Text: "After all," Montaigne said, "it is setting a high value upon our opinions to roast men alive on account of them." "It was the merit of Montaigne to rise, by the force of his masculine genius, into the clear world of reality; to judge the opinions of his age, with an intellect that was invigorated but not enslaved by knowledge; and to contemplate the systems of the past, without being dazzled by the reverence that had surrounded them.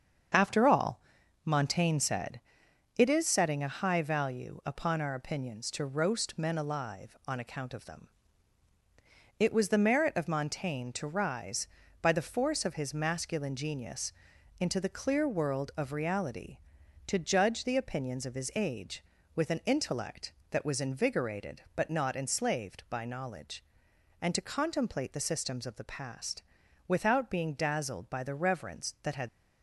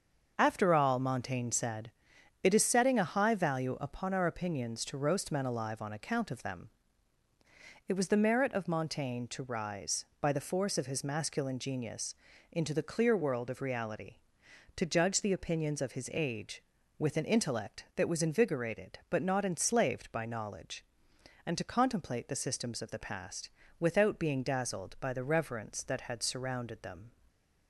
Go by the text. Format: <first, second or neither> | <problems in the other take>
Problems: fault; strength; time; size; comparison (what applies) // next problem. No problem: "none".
second | starts louder than the rest; strong; until 1.7 s; 7 dB; also in the second // stops before "surrounded them"; at 29.2 s